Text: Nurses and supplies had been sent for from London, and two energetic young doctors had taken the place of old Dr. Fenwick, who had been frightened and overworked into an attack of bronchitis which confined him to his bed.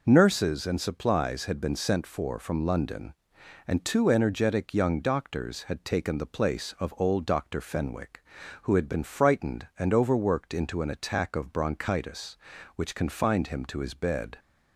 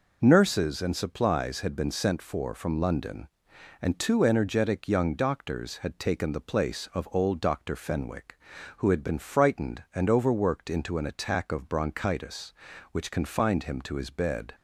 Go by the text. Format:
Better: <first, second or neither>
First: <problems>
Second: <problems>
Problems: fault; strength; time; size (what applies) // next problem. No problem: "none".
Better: neither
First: none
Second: none